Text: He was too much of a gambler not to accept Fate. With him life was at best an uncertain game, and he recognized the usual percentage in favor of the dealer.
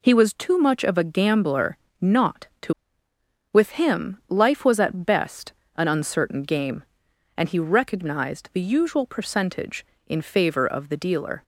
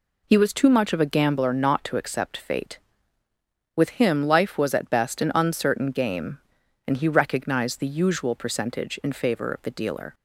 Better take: second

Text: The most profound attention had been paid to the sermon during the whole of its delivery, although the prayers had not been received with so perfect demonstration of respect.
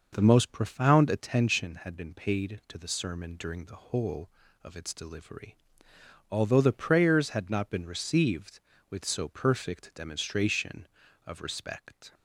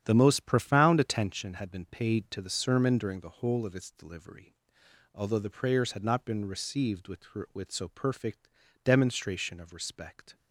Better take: first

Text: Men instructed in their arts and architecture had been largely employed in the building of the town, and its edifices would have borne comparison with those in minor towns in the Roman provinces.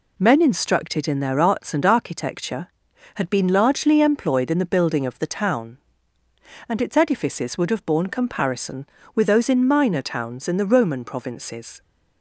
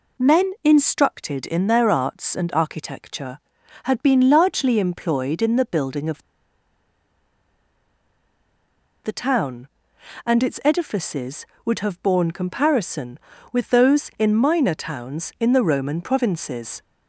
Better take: first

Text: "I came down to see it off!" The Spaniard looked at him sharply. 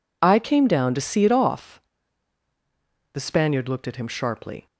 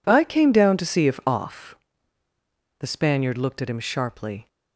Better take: first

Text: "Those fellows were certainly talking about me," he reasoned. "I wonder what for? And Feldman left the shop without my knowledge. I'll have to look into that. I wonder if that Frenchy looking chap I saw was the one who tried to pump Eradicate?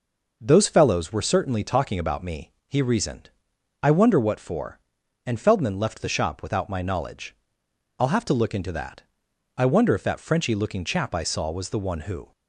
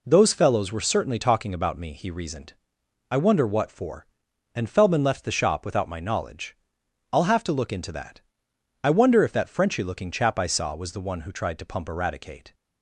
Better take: second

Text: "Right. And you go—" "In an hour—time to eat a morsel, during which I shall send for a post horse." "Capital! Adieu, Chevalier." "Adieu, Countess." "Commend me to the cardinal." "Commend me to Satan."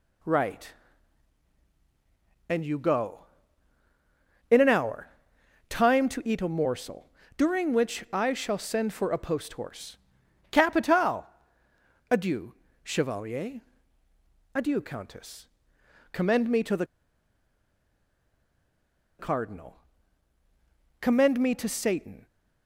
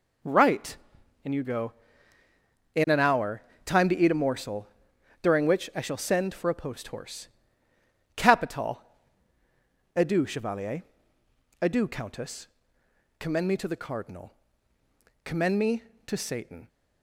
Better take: second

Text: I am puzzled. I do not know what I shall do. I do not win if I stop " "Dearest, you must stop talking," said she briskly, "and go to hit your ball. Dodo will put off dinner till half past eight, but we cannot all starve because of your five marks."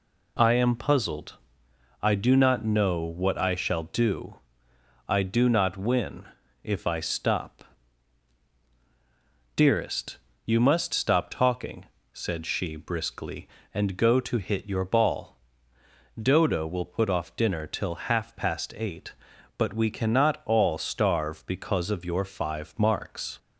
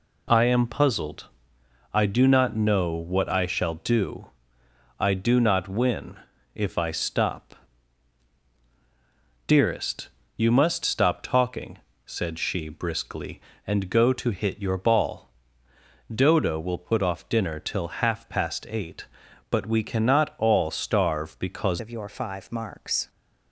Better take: first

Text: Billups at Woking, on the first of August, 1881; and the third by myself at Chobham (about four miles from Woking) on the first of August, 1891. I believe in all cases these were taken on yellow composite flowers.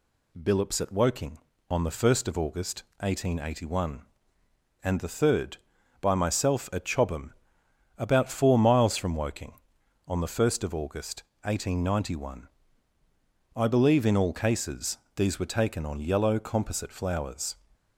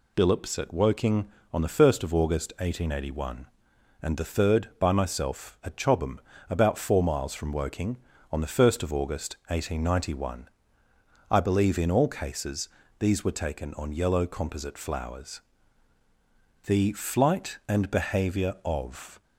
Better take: first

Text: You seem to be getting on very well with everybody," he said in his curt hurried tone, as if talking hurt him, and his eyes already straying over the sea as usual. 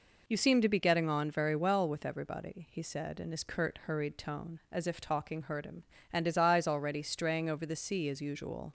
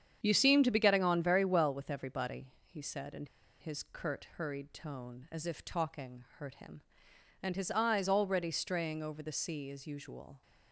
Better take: first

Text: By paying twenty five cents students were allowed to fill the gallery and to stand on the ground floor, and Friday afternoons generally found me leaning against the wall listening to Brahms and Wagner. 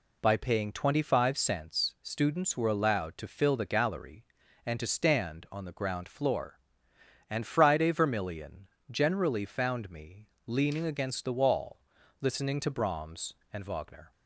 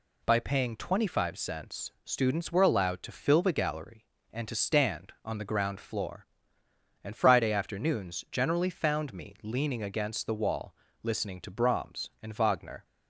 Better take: second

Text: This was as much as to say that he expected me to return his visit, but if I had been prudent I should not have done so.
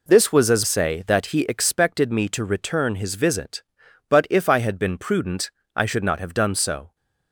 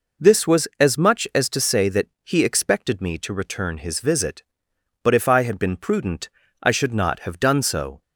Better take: second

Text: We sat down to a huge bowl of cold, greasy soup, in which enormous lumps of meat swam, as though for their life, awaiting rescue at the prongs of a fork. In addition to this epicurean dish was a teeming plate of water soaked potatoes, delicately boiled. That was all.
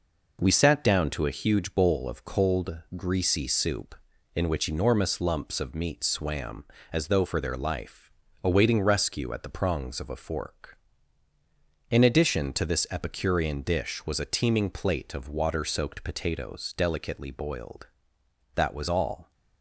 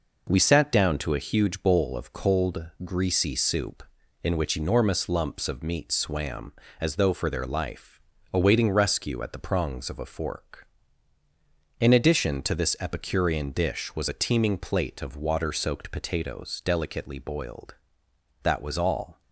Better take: neither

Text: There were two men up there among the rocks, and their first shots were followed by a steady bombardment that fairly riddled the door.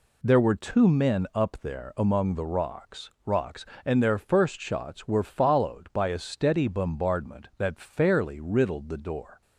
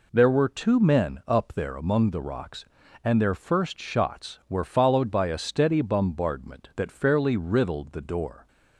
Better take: second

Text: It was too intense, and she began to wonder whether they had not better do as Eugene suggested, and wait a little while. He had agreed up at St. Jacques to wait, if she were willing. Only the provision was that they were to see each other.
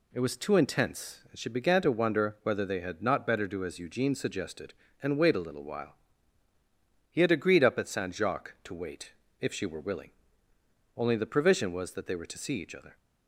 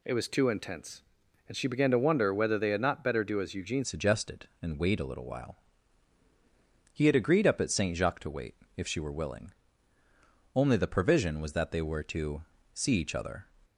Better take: first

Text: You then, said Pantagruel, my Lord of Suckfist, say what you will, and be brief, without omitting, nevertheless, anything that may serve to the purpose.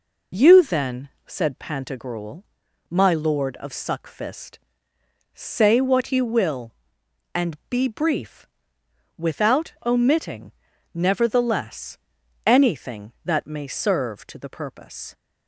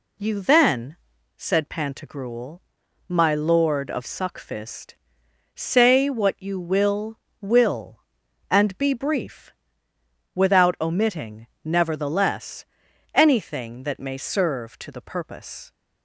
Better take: first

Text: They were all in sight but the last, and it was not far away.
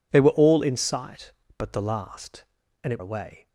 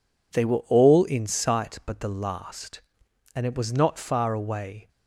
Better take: second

